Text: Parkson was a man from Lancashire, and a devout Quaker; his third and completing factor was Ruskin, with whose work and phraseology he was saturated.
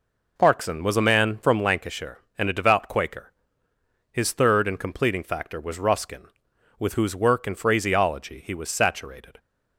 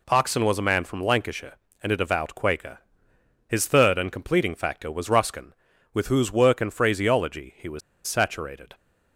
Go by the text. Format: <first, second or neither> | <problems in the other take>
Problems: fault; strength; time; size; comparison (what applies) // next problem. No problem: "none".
first | pauses between "was" and "saturated"; slight; at 7.8 s; 0.26 s long